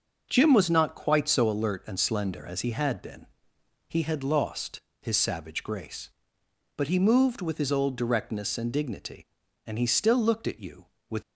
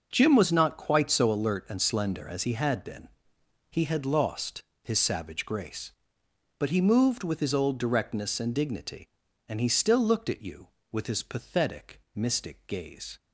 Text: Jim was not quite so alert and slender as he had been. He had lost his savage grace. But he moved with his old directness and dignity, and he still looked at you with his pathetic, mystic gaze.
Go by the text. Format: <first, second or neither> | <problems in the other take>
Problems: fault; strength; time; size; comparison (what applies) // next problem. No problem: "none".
second | starts louder than the rest; noticeable; until 1.3 s; 6 dB; noticeable in the second // pauses between "lost" and "his"; slight; at 4.7 s; 0.24 s long; slight in the second // stops before "his pathetic mystic gaze"; at 11.2 s